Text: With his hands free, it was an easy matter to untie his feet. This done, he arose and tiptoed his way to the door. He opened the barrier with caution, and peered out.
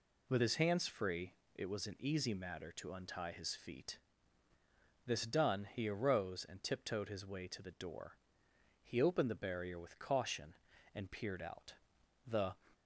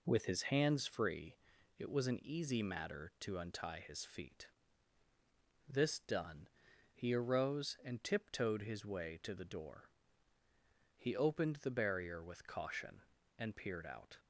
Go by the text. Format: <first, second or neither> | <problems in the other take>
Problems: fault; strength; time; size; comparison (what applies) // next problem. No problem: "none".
second | goes on to say "The"; slight; from 12.2 s on; 0.28 s long